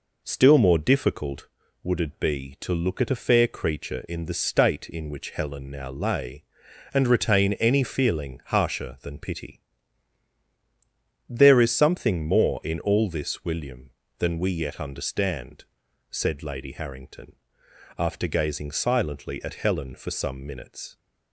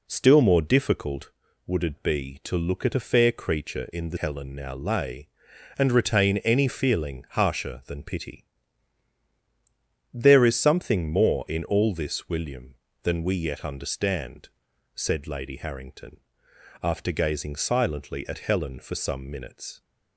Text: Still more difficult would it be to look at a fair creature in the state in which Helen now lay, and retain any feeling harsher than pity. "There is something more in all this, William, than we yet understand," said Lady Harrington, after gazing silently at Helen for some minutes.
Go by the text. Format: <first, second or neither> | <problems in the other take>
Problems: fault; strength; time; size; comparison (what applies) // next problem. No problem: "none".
first | skips "state in which"; at 4.1 s